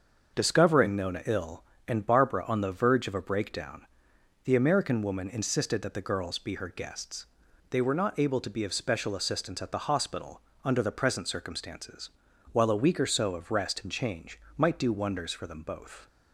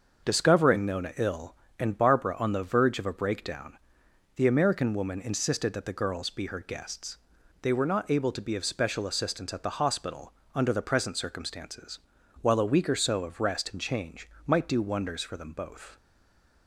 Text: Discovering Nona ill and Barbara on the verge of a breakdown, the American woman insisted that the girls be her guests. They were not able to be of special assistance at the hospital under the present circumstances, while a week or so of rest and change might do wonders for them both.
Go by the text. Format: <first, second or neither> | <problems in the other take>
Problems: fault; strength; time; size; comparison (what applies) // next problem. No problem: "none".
first | starts louder than the rest; until 1.3 s; 6.5 dB; also in the first // pauses between "hospital" and "under"; slight; at 10.3 s; 0.23 s long; slight in the first // pauses between "change" and "might"; slight; at 14.2 s; 0.16 s long; slight in the first // stays silent after the last word; slight; from 15.9 s on; 0.7 s long